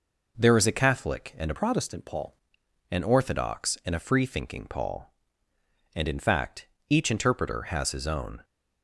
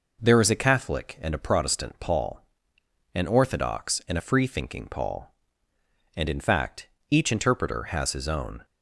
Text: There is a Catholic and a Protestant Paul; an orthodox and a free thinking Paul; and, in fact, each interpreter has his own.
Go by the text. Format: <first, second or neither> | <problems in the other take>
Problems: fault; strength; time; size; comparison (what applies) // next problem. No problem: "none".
second | changes voice from "Protestant" to "Paul"; from 1.5 to 2.3 s; 0.8 s long